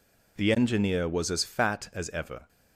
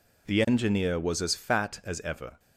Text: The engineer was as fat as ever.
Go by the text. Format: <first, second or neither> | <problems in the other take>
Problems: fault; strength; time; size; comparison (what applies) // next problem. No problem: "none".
neither | none